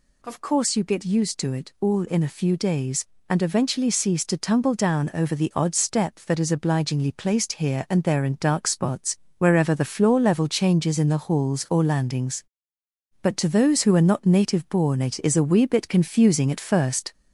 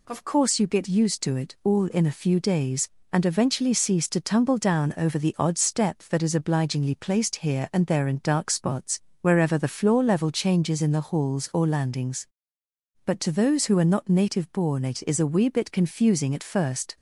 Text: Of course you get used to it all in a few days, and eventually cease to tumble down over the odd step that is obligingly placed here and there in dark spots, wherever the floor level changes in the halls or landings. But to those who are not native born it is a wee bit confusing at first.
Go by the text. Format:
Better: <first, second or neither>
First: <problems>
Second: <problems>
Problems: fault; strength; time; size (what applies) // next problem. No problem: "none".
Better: second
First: gets louder; slight; throughout; 3 dB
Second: none